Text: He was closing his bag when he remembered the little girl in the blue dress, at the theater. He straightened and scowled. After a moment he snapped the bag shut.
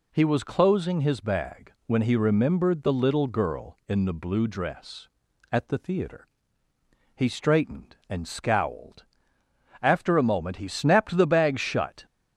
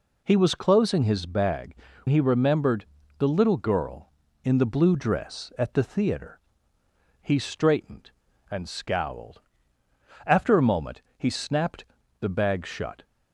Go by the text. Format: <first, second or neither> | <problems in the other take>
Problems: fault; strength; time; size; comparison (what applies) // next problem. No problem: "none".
first | skips "when"; at 1.9 s // pauses between "remembered" and "the"; slight; at 2.8 s; 0.32 s long // pauses between "moment" and "he"; slight; at 11.0 s; 0.16 s long // pauses between "snapped" and "the"; at 11.8 s; 0.38 s long